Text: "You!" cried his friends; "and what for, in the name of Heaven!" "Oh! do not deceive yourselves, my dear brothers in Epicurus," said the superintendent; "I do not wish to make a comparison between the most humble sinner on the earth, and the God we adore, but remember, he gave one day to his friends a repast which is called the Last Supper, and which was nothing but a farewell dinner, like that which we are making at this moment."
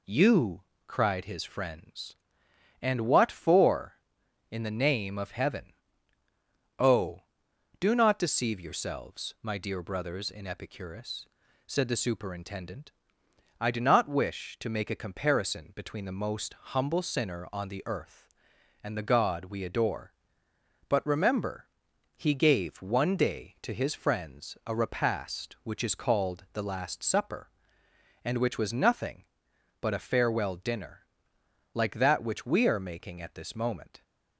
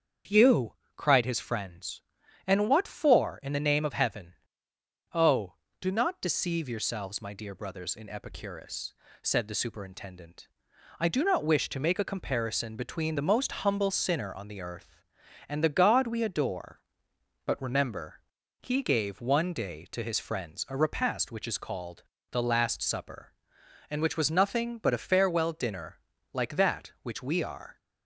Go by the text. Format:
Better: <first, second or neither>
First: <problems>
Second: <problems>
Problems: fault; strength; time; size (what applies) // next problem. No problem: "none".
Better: first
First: none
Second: starts louder than the rest; strong; until 1.4 s; 7.5 dB // pauses between "called" and "the"; slight; at 22.0 s; 0.28 s long // stops before "making at this moment"; at 27.7 s